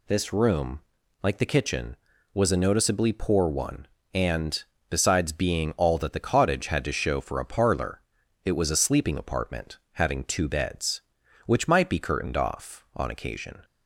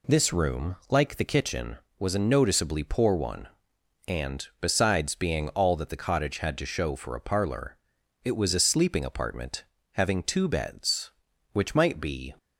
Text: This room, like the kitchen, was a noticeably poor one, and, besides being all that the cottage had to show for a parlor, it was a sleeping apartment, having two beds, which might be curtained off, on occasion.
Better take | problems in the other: first | stops before "curtained off on occasion"; at 12.3 s

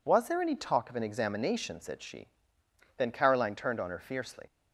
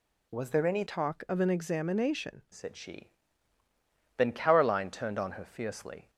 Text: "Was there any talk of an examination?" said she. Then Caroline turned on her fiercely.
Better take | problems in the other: first | changes voice from "talk" to "examination"; from 0.8 to 2.4 s; 1.6 s long

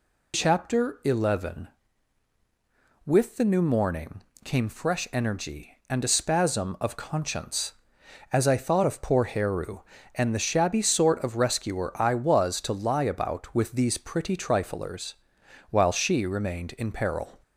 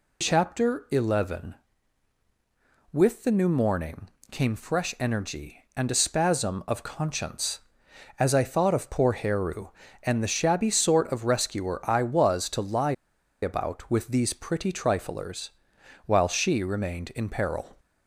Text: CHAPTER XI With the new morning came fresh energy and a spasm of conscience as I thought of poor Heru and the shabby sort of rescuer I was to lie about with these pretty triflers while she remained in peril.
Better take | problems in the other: first | pauses between "morning" and "came"; slight; at 4.0 s; 0.22 s long; slight in the first // pauses between "lie" and "about"; noticeable; at 12.9 s; 0.48 s long // pauses between "triflers" and "while"; noticeable; at 15.4 s; 0.56 s long; noticeable in the first

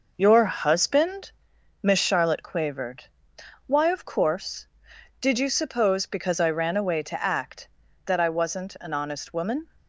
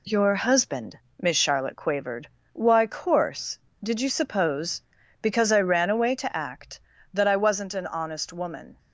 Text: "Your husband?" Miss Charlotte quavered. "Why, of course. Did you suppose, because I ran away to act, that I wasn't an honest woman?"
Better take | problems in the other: first | skips "of"; at 2.8 s

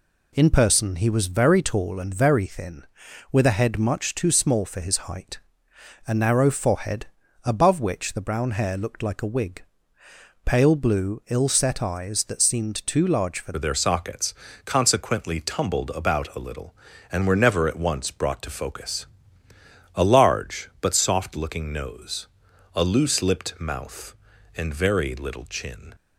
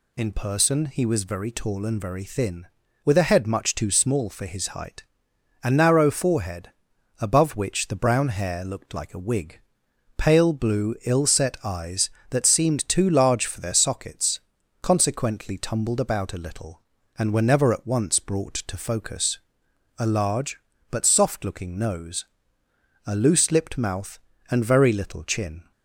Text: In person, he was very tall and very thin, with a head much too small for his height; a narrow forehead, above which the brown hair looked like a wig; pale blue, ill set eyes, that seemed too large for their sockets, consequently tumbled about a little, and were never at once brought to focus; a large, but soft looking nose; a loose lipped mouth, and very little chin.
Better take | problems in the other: second | changes voice at "their"; from 13.5 s on; 12.4 s long

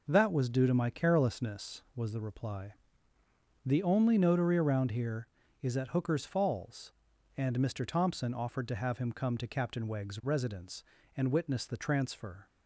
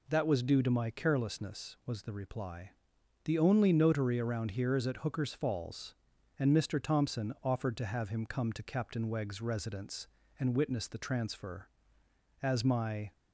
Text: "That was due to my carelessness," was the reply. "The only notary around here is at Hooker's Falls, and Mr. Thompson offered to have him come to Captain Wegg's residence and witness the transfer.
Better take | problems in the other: first | goes on to say "As my"; noticeable; from 12.4 s on; 0.70 s long

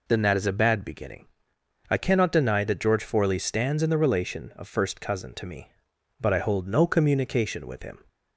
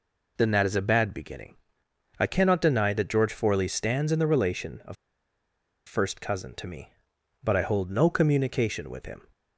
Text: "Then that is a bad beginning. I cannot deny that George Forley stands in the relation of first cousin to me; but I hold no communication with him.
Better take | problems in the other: first | pauses between "of" and "first"; noticeable; at 4.9 s; 0.91 s long

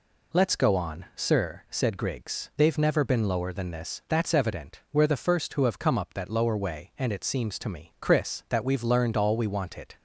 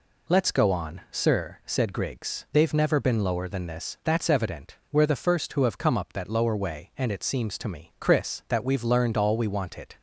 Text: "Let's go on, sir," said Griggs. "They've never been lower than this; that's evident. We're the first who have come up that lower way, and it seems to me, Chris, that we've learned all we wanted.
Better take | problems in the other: neither | none

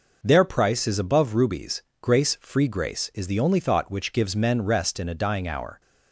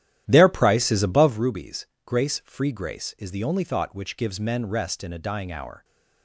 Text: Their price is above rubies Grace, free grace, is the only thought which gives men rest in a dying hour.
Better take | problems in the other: first | starts louder than the rest; strong; until 1.4 s; 12 dB // pauses between "rubies" and "Grace"; slight; at 1.8 s; 0.18 s long; slight in the first

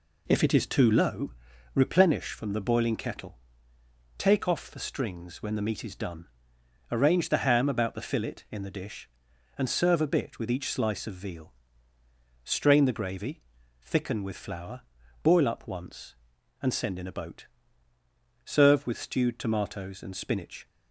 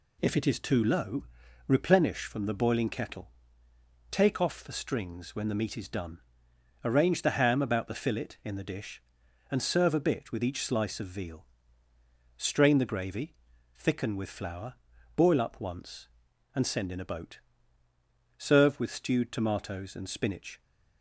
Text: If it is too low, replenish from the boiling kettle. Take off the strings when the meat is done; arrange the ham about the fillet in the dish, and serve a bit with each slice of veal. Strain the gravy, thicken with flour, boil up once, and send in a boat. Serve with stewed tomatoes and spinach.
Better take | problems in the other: second | starts louder than the rest; slight; until 1.2 s; 2.5 dB

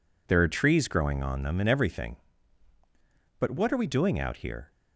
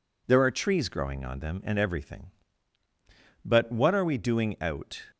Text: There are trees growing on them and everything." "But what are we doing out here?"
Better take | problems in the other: first | stops before "here"; at 5.1 s

